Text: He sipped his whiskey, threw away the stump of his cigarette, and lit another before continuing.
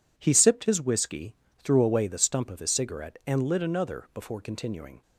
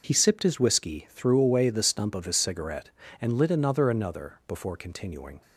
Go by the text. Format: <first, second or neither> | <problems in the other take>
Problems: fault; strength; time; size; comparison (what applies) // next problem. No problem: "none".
first | says "another" twice; at 3.8 s